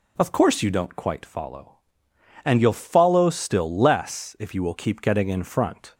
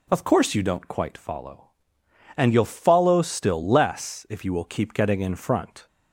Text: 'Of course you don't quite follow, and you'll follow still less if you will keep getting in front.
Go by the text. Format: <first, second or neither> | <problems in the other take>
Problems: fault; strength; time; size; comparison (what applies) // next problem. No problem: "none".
neither | none